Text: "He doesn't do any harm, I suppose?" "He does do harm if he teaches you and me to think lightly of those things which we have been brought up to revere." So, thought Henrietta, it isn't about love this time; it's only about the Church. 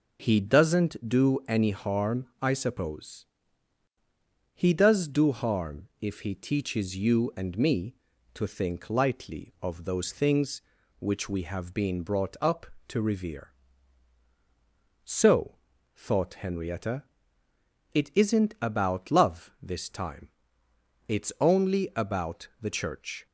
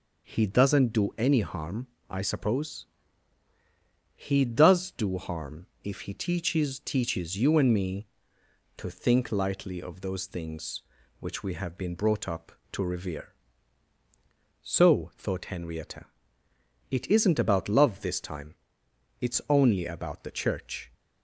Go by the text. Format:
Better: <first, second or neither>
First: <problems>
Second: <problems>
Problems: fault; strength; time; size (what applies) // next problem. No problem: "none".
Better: first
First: none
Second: pauses between "harm" and "if"; slight; at 5.6 s; 0.16 s long // says "teaches" twice; at 6.7 s